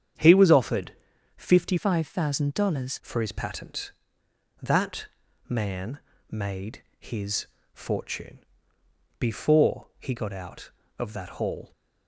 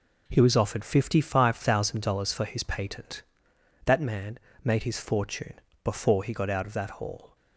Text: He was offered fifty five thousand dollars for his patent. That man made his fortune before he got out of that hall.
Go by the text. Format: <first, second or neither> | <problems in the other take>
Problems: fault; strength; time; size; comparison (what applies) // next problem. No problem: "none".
second | starts louder than the rest; strong; until 1.6 s; 8.5 dB // pauses between "offered" and "fifty"; at 0.9 s; 0.44 s long // changes voice from "five" to "dollars"; from 1.7 to 3.0 s; 1.3 s long // pauses between "That" and "man"; at 5.0 s; 0.40 s long // pauses between "man" and "made"; slight; at 5.9 s; 0.32 s long; slight in the second // pauses between "made" and "his"; slight; at 6.8 s; 0.16 s long // pauses between "his" and "fortune"; slight; at 7.4 s; 0.28 s long // pauses between "fortune" and "before"; noticeable; at 8.3 s; 0.80 s long; slight in the second